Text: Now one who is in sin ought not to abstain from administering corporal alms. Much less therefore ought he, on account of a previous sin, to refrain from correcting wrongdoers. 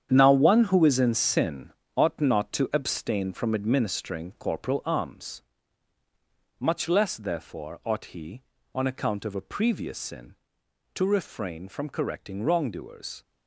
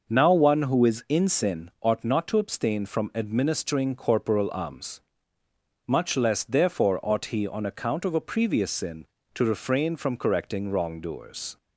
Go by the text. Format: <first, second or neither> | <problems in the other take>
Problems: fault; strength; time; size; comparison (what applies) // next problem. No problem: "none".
second | gets quieter; strong; throughout; 10 dB // pauses between "sin" and "ought"; slight; at 1.6 s; 0.26 s long